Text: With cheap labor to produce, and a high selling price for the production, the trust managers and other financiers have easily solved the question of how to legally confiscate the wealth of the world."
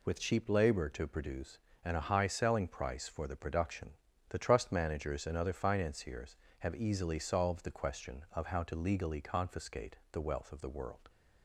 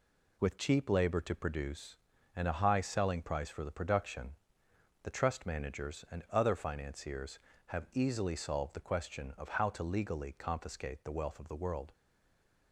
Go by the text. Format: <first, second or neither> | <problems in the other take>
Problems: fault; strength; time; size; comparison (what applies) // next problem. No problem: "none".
first | stays silent after the last word; slight; from 11.9 s on; 0.8 s long